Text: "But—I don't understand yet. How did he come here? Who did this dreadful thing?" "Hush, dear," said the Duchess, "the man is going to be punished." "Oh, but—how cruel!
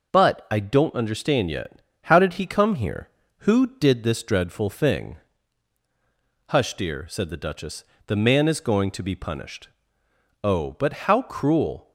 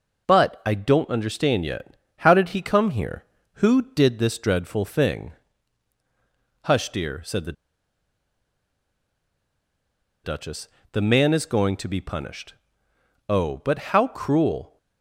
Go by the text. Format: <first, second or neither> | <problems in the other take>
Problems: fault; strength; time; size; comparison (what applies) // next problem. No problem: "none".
first | pauses between "the" and "Duchess"; strong; at 7.5 s; 2.7 s long